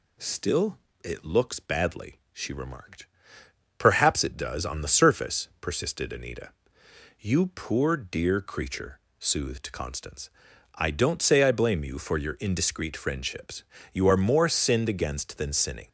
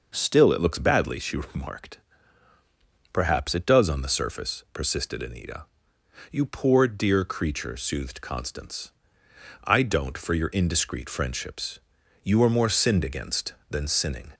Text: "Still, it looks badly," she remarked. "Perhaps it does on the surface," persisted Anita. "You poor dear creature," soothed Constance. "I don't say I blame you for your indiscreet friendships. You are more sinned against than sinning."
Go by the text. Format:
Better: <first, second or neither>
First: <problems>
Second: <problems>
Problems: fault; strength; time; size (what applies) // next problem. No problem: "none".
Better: first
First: none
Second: skips "say I blame you"; at 10.1 s